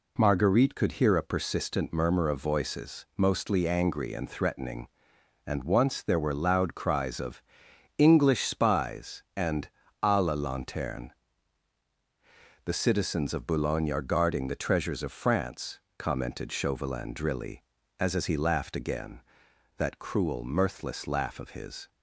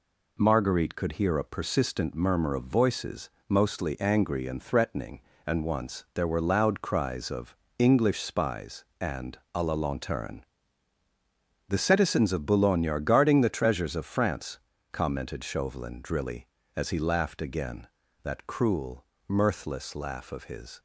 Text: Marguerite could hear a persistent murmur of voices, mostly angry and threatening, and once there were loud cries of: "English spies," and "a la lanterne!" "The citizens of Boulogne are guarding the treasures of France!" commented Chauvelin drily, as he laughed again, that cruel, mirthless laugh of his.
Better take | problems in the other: second | pauses between "and" and "a"; slight; at 9.6 s; 0.34 s long; slight in the second // says "as" twice; at 18.1 s

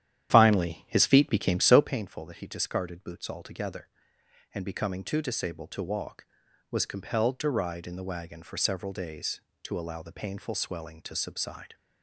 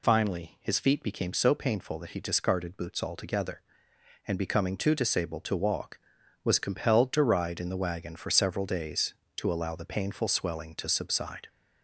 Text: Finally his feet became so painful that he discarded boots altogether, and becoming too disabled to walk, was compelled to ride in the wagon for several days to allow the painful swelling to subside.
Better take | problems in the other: second | starts louder than the rest; strong; until 2.0 s; 10.5 dB

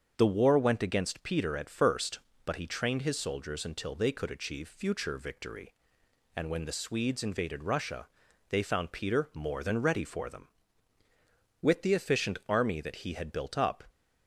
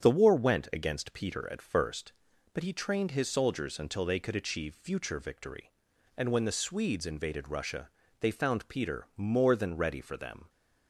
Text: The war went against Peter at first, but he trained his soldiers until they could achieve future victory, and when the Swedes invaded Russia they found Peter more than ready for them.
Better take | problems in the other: second | starts louder than the rest; until 1.1 s; 7 dB; strong in the second // pauses between "Russia" and "they"; at 8.0 s; 0.42 s long; slight in the second // goes on to say "With the efficient army that he had built up"; strong; from 11.6 s on; 2.2 s long

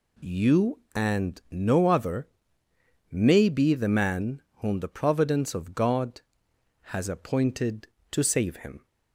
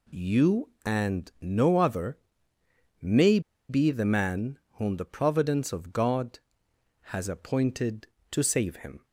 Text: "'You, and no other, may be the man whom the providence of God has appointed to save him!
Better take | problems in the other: first | pauses between "may" and "be"; slight; at 3.3 s; 0.29 s long // pauses between "man" and "whom"; slight; at 4.5 s; 0.16 s long; slight in the first

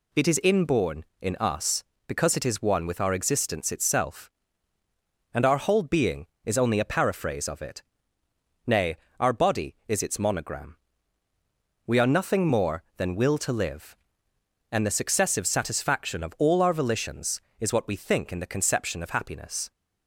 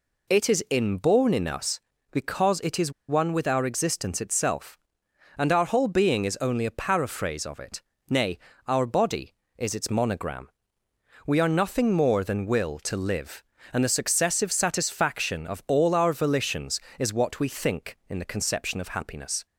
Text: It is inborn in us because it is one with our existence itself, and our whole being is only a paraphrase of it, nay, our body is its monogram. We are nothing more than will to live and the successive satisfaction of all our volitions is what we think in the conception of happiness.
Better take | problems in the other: first | pauses between "is" and "one"; slight; at 2.9 s; 0.16 s long

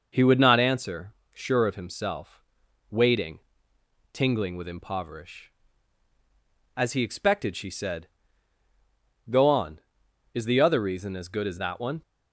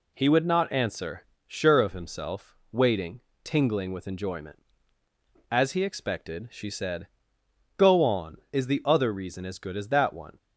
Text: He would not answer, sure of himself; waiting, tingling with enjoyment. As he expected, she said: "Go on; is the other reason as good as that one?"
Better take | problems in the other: second | says "impoverish" for "enjoyment"; at 4.6 s

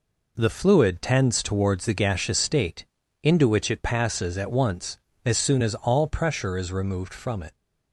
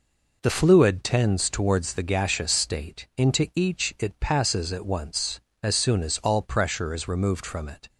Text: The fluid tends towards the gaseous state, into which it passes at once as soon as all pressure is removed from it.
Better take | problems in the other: first | says "each" for "which"; at 3.5 s

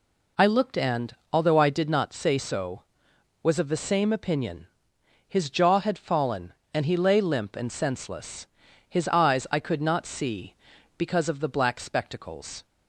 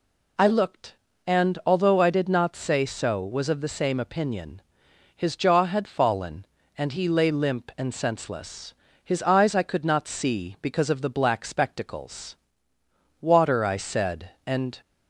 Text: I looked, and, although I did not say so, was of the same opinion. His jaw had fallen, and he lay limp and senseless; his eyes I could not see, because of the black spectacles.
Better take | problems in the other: first | goes on to say "Water I said and"; from 13.2 s on; 1.5 s long

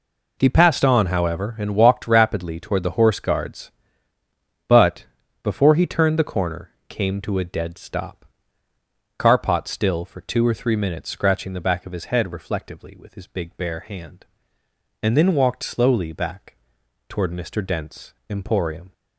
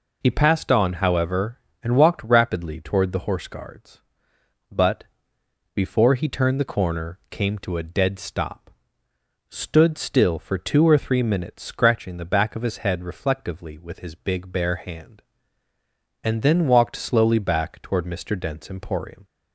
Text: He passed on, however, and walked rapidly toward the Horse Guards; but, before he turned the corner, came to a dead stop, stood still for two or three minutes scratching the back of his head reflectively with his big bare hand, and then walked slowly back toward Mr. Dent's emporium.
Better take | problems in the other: second | says "carpot" for "stood"; at 9.1 s // pauses between "back" and "toward"; noticeable; at 16.5 s; 0.54 s long // pauses between "Dent's" and "emporium"; slight; at 18.1 s; 0.16 s long

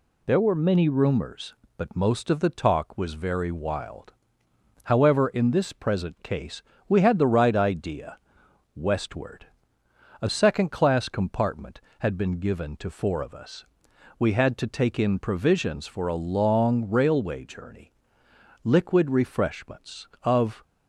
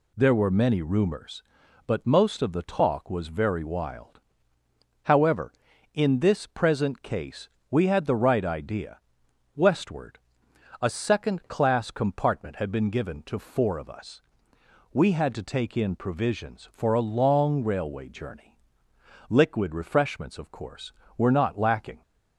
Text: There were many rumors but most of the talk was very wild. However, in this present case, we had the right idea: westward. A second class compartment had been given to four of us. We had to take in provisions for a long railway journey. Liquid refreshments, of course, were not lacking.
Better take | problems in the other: second | stops before "course were not lacking"; at 20.6 s

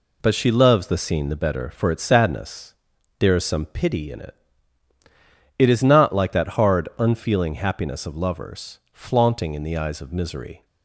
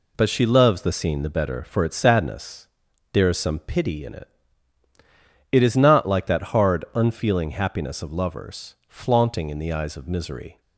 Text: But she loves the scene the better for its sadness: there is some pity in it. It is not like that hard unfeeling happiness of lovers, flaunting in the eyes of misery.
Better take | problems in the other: neither | none

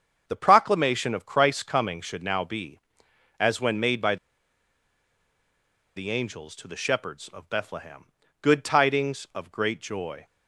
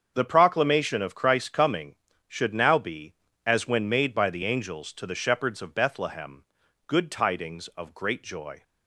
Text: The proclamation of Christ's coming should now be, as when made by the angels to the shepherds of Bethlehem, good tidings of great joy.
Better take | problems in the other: second | starts louder than the rest; until 1.2 s; 7 dB; strong in the second // pauses between "by" and "the"; strong; at 4.1 s; 1.8 s long

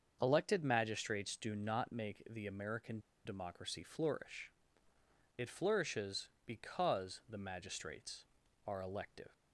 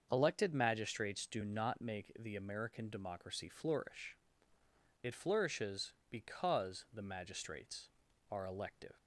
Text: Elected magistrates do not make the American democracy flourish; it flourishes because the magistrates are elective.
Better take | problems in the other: second | starts louder than the rest; until 1.2 s; 6.5 dB; also in the second // pauses between "American" and "democracy"; slight; at 2.9 s; 0.26 s long

